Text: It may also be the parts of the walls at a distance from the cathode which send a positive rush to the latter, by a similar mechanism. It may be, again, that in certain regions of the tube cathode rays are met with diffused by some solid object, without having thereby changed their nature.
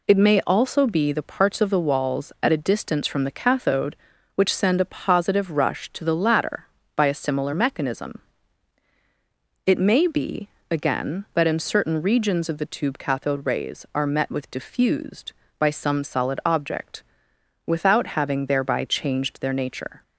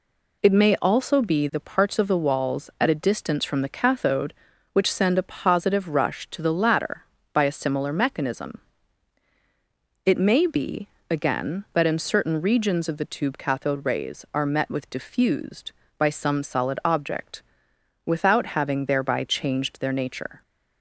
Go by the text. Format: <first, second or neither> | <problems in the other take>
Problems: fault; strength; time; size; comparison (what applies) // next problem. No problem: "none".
neither | none